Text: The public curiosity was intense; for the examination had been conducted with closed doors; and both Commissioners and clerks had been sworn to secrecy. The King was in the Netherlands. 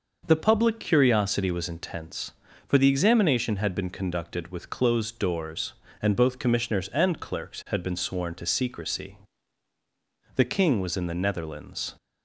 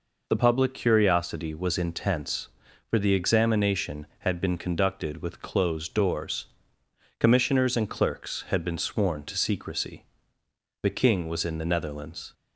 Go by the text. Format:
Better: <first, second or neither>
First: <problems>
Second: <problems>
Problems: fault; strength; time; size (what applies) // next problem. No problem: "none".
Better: first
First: none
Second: skips "and both"; at 6.8 s